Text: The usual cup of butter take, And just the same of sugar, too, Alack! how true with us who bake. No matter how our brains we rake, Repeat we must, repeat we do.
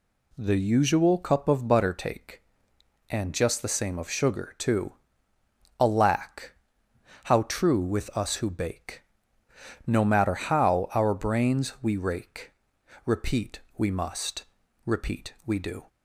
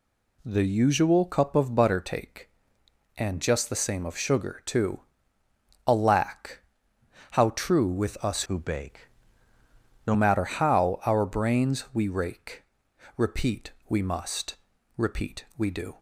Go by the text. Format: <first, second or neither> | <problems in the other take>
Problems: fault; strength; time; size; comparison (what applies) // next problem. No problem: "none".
first | changes voice from "who" to "No"; from 8.4 to 10.1 s; 1.7 s long // pauses between "Repeat" and "we"; slight; at 13.7 s; 0.18 s long; slight in the first